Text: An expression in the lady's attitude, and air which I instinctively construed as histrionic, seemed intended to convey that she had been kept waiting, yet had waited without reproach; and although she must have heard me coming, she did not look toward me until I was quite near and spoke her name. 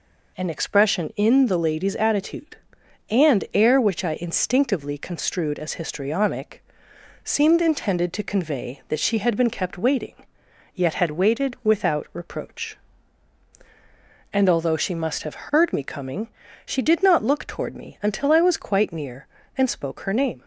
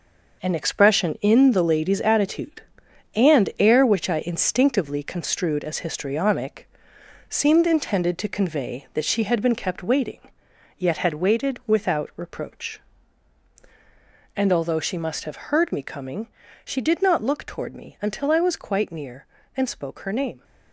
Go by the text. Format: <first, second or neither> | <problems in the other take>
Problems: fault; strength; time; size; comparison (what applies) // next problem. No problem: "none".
first | gets quieter; strong; throughout; 8 dB